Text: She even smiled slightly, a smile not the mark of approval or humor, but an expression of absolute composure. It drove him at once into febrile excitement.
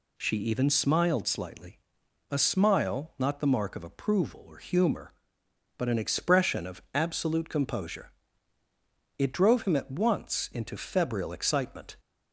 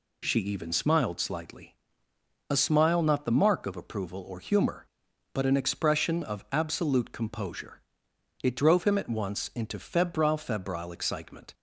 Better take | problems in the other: first | says "febrile" twice; at 10.3 s

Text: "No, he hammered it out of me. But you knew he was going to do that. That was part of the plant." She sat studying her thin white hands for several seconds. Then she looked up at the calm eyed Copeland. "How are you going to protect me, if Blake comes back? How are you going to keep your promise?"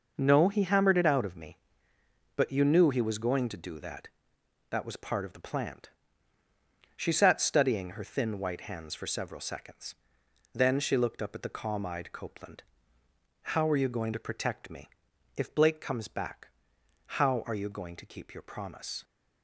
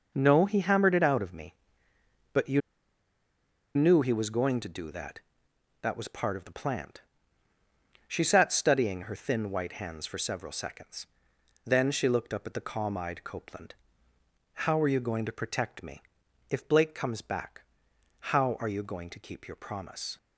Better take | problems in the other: first | pauses between "you" and "knew"; at 2.6 s; 1.1 s long

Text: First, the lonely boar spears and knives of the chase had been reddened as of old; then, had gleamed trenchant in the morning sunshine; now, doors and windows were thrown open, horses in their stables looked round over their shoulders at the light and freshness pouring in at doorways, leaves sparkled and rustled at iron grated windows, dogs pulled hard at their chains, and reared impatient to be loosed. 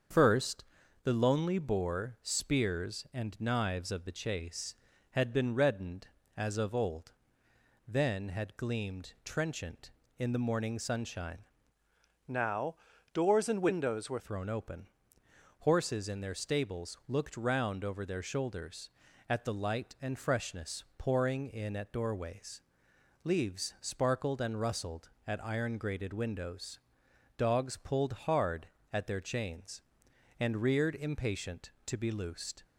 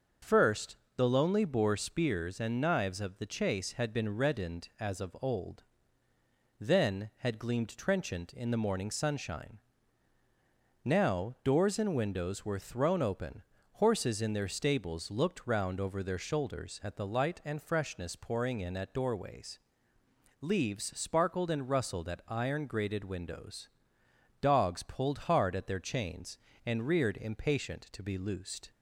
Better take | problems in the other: second | starts louder than the rest; until 1.5 s; 7 dB; also in the second // changes voice from "now" to "were"; from 12.2 to 14.1 s; 1.9 s long // pauses between "freshness" and "pouring"; slight; at 20.8 s; 0.16 s long

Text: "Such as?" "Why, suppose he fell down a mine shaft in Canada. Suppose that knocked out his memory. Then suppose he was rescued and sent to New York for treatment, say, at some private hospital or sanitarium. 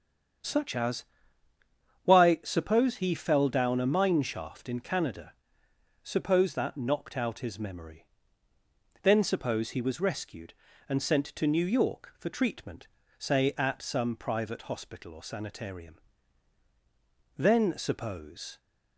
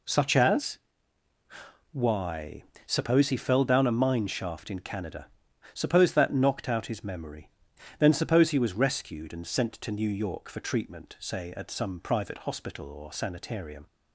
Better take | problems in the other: second | starts louder than the rest; strong; until 2.4 s; 8 dB // goes on to say "Then suppose"; noticeable; from 17.3 s on; 1.2 s long

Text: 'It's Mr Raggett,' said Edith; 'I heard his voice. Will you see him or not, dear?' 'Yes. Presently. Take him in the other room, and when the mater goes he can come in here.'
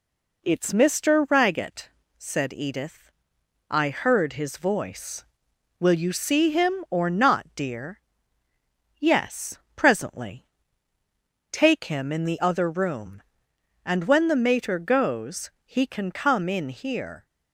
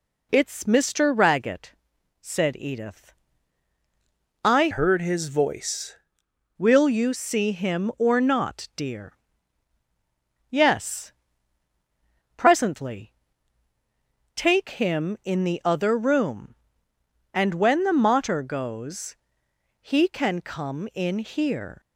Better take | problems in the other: first | changes voice from "heard" to "voice"; from 4.7 to 5.9 s; 1.2 s long // pauses between "goes" and "he"; noticeable; at 19.1 s; 0.64 s long; slight in the first

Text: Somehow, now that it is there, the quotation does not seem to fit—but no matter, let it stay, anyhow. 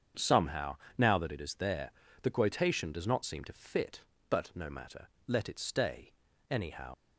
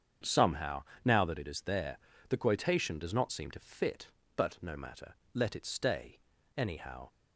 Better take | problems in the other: second | starts louder than the rest; strong; until 1.3 s; 7.5 dB; strong in the second // leaves "anyhow" unfinished; at 6.9 s; 80 ms

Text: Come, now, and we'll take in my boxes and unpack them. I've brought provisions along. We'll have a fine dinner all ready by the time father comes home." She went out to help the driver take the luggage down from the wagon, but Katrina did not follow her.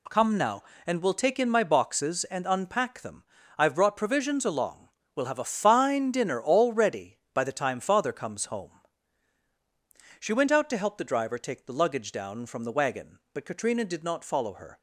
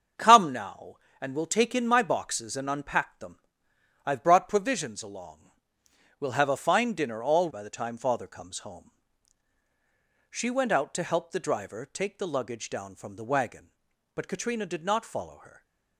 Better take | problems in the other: first | starts louder than the rest; strong; until 1.4 s; 7 dB // skips "ready"; at 7.4 s // stays silent after the last word; slight; from 15.4 s on; 0.5 s long

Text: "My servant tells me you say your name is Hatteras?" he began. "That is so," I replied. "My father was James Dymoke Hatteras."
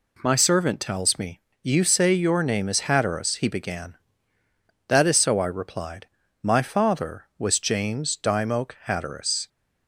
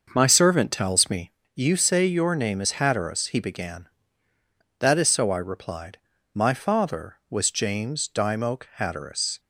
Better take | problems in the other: first | starts louder than the rest; noticeable; until 1.5 s; 6 dB // pauses between "me" and "you"; slight; at 1.3 s; 0.24 s long; slight in the first

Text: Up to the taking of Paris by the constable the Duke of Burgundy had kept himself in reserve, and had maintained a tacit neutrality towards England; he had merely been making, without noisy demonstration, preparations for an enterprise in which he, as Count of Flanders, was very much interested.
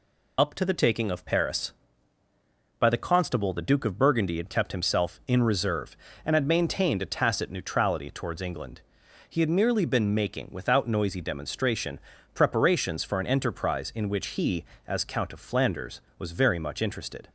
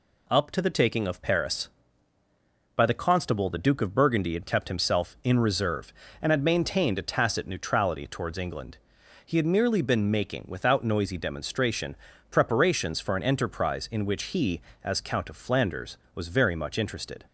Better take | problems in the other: second | loses the start of "Up"; at 0.3 s; 70 ms

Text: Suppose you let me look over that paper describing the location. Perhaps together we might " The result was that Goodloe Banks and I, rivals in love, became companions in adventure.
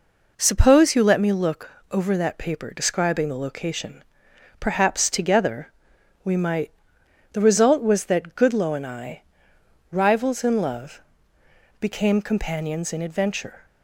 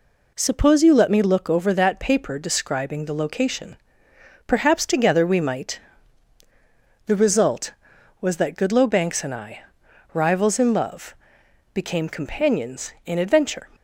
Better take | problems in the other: second | pauses between "look" and "over"; slight; at 1.7 s; 0.20 s long // pauses between "together" and "we"; noticeable; at 5.7 s; 0.54 s long // skips "Banks"; at 8.7 s

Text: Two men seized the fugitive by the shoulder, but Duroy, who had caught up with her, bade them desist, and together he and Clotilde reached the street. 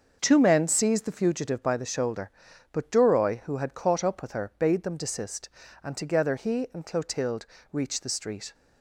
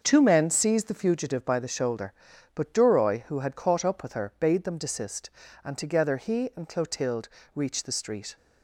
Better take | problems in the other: neither | starts louder than the rest; the same in both // pauses between "Clotilde" and "reached"; slight; the same in both

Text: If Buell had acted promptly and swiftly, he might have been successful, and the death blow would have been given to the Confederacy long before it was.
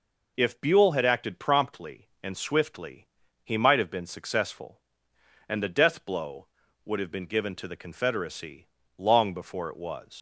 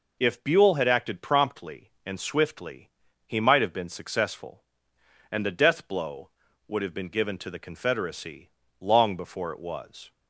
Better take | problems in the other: second | pauses between "Confederacy" and "long"; slight; at 8.6 s; 0.30 s long; slight in the second // leaves "was" unfinished; at 10.1 s; 90 ms

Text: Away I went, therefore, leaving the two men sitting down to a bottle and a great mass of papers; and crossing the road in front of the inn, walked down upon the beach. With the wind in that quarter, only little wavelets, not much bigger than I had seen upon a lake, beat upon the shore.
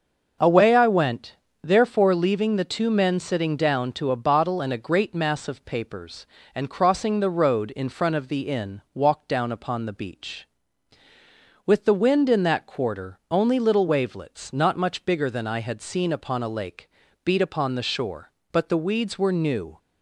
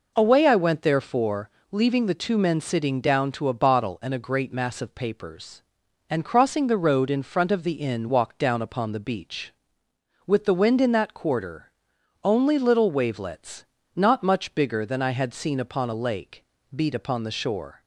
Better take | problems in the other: second | starts louder than the rest; noticeable; until 1.7 s; 6 dB // goes on to say "But the weeds were new"; noticeable; from 18.5 s on; 1.2 s long

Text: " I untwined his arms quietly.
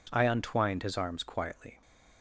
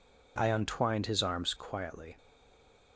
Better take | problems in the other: first | stays silent after the last word; slight; from 2.1 s on; 0.8 s long

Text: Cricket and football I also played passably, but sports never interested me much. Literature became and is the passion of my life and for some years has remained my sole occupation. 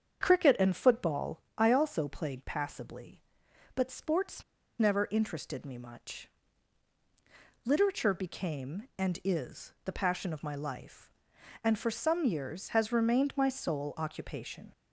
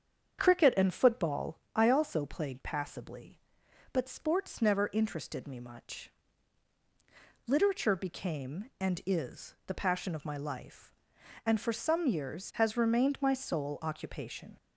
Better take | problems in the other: second | starts louder than the rest; strong; until 1.2 s; 7.5 dB; strong in the second // pauses between "football" and "I"; slight; at 1.4 s; 0.16 s long; slight in the second // pauses between "sports" and "never"; at 4.4 s; 0.36 s long

